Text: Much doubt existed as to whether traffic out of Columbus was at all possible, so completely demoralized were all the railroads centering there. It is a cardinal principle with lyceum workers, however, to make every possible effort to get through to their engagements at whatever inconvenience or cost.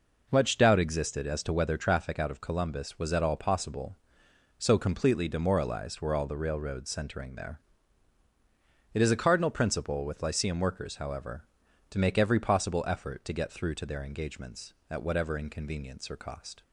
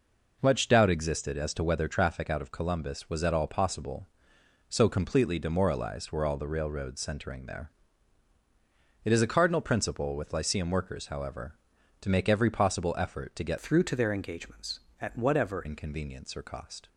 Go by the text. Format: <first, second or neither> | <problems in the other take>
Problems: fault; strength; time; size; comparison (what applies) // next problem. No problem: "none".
first | changes voice from "through" to "whatever"; from 13.5 to 15.6 s; 2.1 s long